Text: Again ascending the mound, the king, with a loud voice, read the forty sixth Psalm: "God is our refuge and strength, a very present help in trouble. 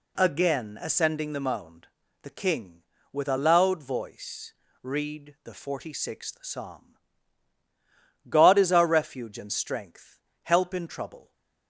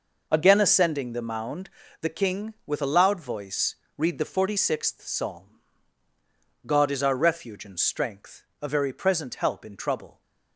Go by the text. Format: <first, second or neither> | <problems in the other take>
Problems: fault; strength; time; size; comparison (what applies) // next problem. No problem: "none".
second | skips "a very present"; at 10.3 s